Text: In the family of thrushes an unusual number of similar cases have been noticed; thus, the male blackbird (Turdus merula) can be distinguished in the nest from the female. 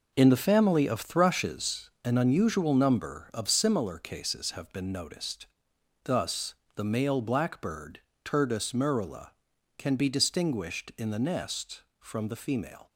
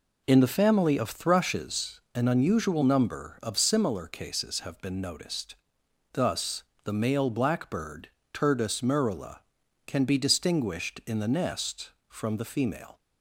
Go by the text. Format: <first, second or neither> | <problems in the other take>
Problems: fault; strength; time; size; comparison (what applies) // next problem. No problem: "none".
second | gets quieter; strong; throughout; 9.5 dB